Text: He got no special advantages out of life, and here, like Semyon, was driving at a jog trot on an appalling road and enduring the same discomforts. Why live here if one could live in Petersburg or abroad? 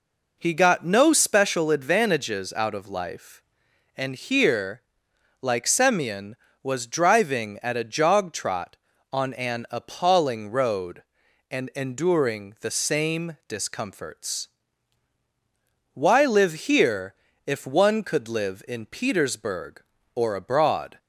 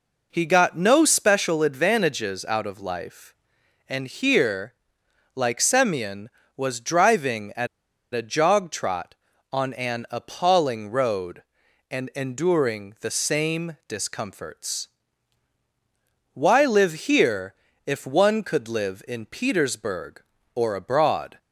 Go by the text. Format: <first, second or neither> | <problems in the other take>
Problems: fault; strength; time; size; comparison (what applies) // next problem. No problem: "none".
first | pauses between "at" and "a"; noticeable; at 7.6 s; 0.46 s long // pauses between "here" and "if"; slight; at 17.5 s; 0.32 s long; slight in the first